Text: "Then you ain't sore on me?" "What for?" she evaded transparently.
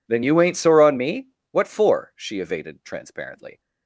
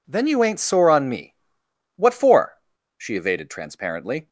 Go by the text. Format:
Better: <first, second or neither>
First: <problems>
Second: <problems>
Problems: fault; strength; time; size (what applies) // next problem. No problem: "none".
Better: neither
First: none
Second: none